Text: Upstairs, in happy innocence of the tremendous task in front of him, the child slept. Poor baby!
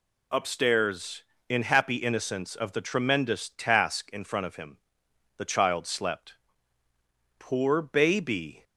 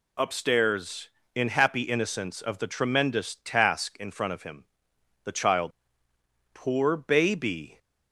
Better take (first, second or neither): first